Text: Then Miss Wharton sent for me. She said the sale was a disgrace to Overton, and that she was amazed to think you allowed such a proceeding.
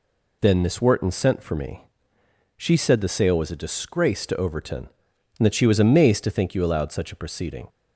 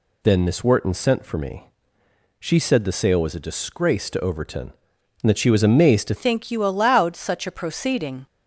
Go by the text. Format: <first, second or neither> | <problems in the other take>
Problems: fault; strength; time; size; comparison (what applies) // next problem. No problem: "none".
first | changes voice at "think"; from 6.1 s on; 2.1 s long